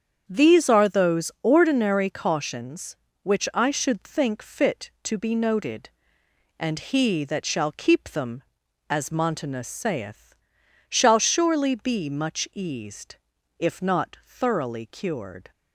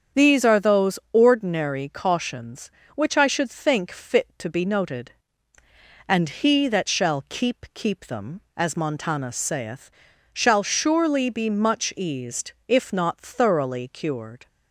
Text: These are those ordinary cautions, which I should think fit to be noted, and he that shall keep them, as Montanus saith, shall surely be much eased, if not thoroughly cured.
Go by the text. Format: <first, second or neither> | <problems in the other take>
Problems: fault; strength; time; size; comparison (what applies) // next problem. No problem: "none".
first | starts louder than the rest; strong; until 1.3 s; 7.5 dB; strong in the first // pauses between "those" and "ordinary"; slight; at 0.9 s; 0.16 s long // says "keep" twice; at 7.7 s